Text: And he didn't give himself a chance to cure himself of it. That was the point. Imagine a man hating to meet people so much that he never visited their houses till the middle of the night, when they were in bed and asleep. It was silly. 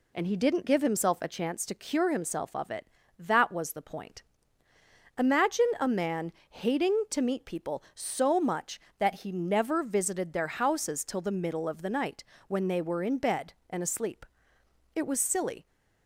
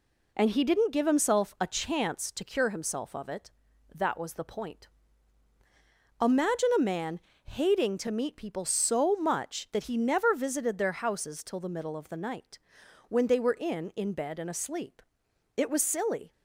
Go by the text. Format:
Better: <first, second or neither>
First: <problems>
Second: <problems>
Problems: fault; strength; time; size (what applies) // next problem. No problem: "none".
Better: first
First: pauses between "man" and "hating"; slight; at 6.3 s; 0.18 s long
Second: pauses between "man" and "hating"; slight; at 7.1 s; 0.26 s long // says "in" twice; at 13.9 s